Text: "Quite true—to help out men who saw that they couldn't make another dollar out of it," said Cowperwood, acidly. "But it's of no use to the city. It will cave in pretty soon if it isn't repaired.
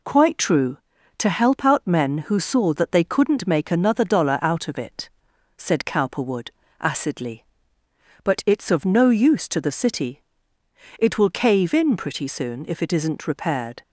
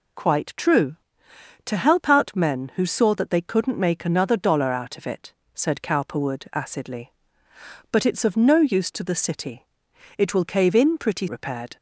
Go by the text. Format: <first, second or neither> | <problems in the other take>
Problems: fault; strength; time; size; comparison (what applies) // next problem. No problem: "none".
first | skips "soon if it isn't"; at 11.2 s